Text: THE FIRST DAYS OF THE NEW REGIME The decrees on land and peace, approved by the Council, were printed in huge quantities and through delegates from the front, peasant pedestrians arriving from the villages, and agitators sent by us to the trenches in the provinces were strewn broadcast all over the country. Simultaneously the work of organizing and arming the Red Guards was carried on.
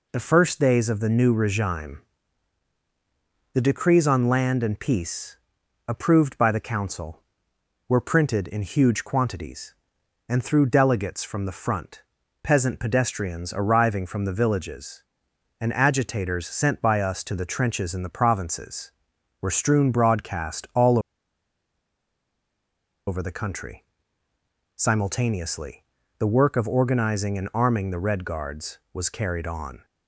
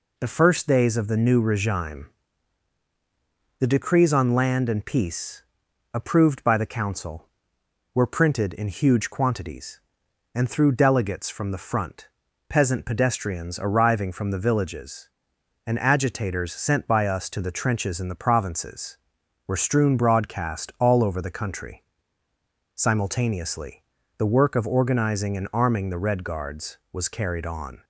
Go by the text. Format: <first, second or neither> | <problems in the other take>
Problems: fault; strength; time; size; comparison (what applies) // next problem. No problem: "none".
second | pauses between "REGIME" and "The"; strong; at 2.0 s; 1.5 s long; strong in the second // pauses between "all" and "over"; strong; at 20.9 s; 2.0 s long // pauses between "Simultaneously" and "the"; slight; at 25.8 s; 0.36 s long; slight in the second